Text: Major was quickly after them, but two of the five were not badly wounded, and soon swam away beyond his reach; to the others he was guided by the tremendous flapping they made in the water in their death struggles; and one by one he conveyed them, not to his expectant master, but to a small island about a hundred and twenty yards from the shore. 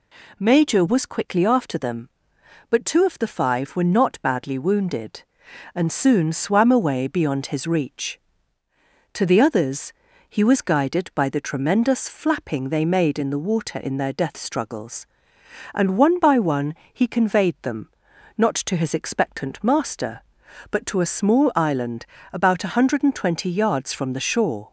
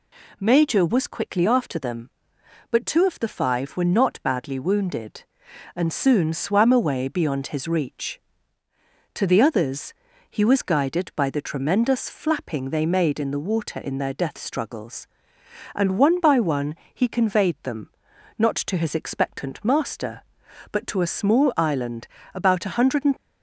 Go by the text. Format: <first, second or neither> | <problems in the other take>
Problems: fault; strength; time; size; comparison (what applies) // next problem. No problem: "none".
first | pauses between "others" and "he"; slight; at 9.9 s; 0.36 s long; slight in the first // pauses between "one" and "he"; slight; at 16.7 s; 0.20 s long; slight in the first // pauses between "island" and "about"; slight; at 22.0 s; 0.26 s long; slight in the first // stops before "twenty yards from the shore"; at 23.1 s